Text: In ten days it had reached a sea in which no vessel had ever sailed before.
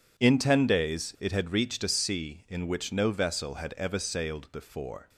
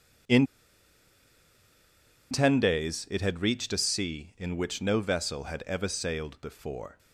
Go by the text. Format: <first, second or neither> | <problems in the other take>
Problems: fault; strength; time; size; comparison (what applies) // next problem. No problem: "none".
first | pauses between "In" and "ten"; strong; at 0.4 s; 1.8 s long